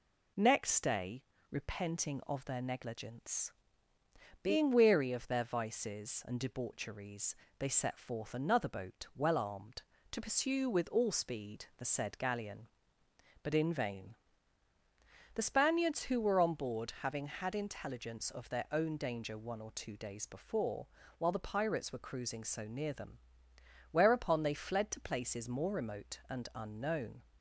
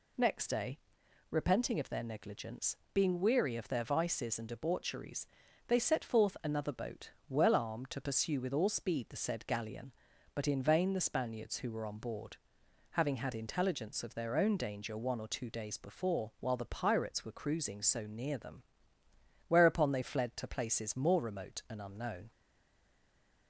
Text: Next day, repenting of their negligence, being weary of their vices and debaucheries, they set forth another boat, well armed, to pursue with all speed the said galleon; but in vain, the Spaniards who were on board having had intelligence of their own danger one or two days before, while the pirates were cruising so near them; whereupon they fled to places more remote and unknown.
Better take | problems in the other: first | pauses between "board" and "having"; noticeable; at 12.3 s; 0.56 s long // stays silent after the last word; noticeable; from 22.3 s on; 1.1 s long

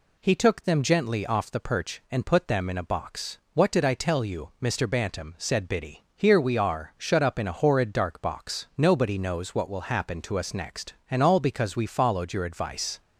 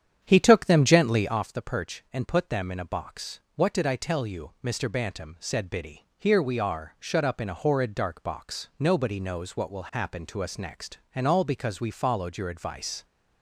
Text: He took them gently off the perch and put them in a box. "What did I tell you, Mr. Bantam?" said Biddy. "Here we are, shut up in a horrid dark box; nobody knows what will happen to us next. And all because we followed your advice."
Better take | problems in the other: first | starts louder than the rest; strong; until 1.4 s; 9 dB

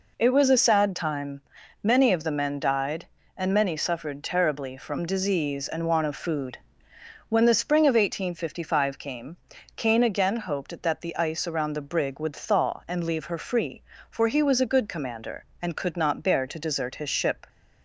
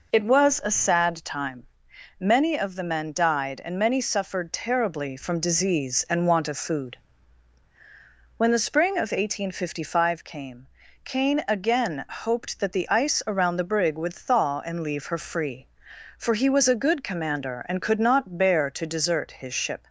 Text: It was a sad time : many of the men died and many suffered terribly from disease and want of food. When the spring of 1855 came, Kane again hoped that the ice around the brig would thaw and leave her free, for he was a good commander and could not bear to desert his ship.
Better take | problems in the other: neither | none

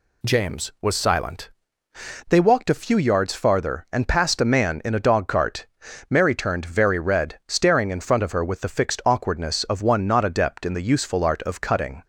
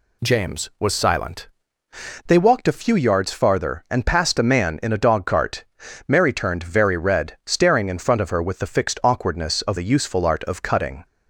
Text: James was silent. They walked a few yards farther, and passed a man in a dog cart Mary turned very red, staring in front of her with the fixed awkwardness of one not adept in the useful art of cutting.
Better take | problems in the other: first | pauses between "cart" and "Mary"; noticeable; at 5.6 s; 0.46 s long; noticeable in the first // skips "one not adept in"; at 9.7 s

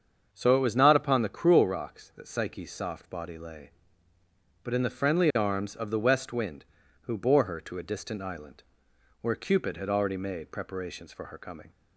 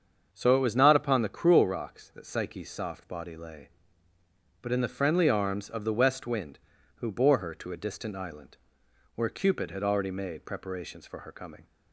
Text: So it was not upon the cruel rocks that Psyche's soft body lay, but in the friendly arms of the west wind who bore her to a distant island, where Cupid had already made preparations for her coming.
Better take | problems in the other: neither | starts louder than the rest; the same in both

